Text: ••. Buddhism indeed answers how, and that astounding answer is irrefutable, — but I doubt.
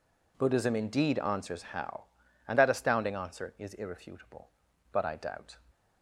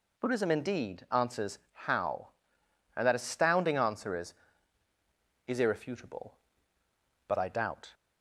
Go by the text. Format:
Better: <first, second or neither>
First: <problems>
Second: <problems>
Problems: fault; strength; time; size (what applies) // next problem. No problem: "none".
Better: first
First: none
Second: says "is" twice; at 5.4 s